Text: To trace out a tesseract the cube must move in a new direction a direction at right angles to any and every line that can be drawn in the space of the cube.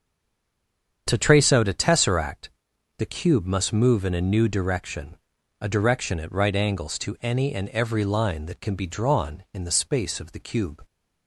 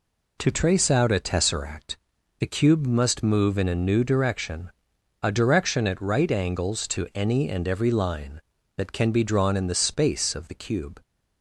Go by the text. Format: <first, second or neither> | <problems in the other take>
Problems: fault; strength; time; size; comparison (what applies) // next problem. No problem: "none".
second | stays silent before the first word; until 1.0 s; 1.0 s long // starts louder than the rest; strong; until 2.0 s; 7.5 dB // pauses between "tesseract" and "the"; noticeable; at 2.4 s; 0.48 s long; also in the second // pauses between "direction" and "a"; at 5.1 s; 0.42 s long; noticeable in the second